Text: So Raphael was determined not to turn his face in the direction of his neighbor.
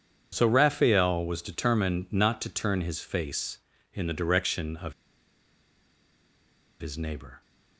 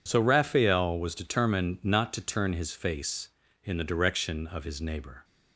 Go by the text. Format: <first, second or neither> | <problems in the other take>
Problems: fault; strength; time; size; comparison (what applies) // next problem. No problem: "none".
second | pauses between "of" and "his"; strong; at 4.9 s; 1.8 s long